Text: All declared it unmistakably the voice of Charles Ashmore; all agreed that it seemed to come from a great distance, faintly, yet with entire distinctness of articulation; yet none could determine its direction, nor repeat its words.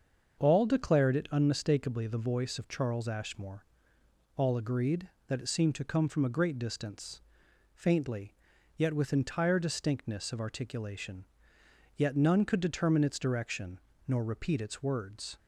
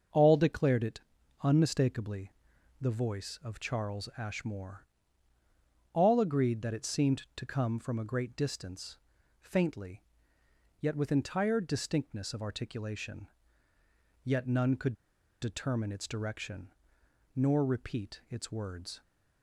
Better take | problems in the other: first | starts louder than the rest; until 1.5 s; 6.5 dB; also in the first // pauses between "it" and "unmistakably"; at 0.9 s; 0.42 s long // pauses between "unmistakably" and "the"; noticeable; at 2.3 s; 0.48 s long // pauses between "could" and "determine"; noticeable; at 14.9 s; 0.47 s long

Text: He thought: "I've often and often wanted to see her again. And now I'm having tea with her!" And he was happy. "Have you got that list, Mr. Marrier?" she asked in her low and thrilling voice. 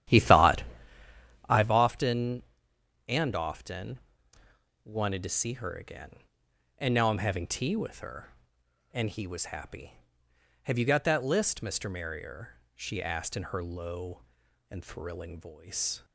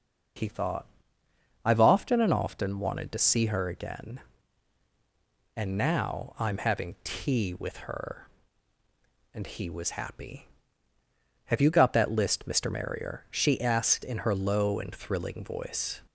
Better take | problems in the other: second | starts louder than the rest; strong; until 1.7 s; 11.5 dB // pauses between "often" and "wanted"; noticeable; at 3.9 s; 0.84 s long

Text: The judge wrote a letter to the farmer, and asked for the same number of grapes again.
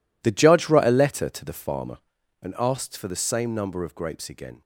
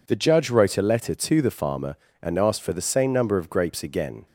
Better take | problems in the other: second | gets quieter; strong; throughout; 15 dB

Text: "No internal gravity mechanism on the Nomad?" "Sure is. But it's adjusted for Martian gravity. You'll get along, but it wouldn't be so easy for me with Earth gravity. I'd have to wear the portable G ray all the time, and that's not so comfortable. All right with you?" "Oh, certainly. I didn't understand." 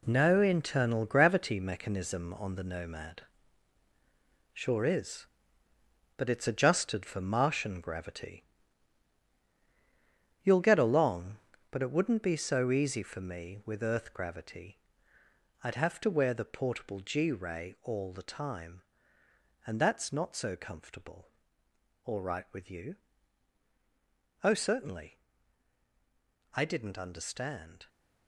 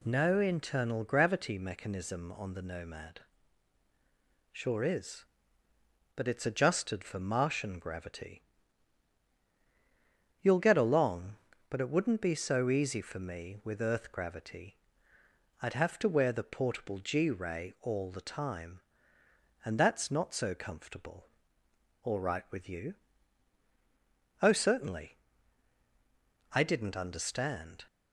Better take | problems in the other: second | gets quieter; strong; throughout; 9 dB

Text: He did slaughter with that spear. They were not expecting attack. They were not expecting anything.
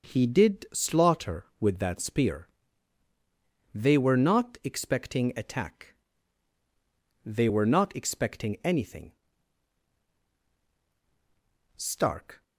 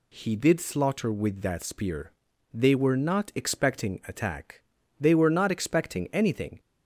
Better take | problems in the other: second | goes on to say "Stark"; noticeable; from 11.7 s on; 0.66 s long

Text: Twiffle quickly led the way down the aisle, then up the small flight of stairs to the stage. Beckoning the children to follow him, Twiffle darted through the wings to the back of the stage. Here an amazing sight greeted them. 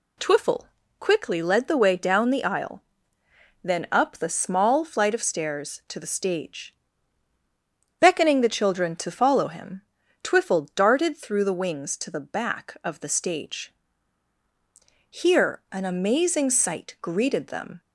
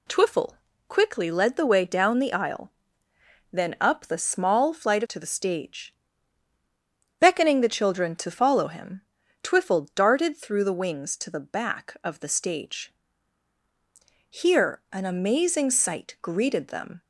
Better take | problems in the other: first | pauses between "Twiffle" and "quickly"; slight; at 0.5 s; 0.32 s long; slight in the first // skips "of stairs"; at 5.0 s

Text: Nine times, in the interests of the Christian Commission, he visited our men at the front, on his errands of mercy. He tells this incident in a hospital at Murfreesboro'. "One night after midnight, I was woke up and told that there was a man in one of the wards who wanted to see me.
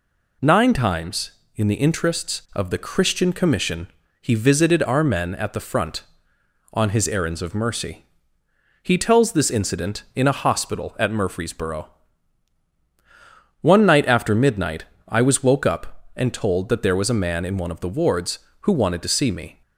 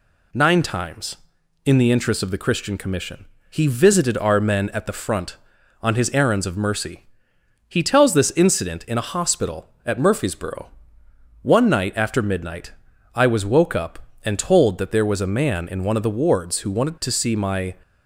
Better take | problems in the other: first | says "my" for "me"; at 17.3 s

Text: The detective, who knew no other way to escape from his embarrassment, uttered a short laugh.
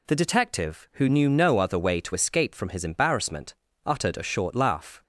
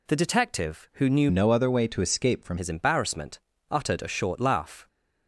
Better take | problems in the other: first | changes voice from "no" to "from"; from 1.3 to 2.5 s; 1.2 s long

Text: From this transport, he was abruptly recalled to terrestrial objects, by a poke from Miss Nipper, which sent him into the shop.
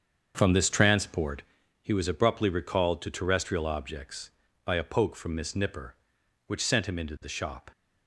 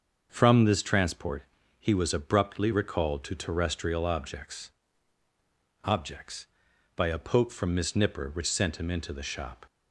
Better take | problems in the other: first | starts louder than the rest; until 1.3 s; 6.5 dB; also in the first // says "objects" twice; at 5.8 s

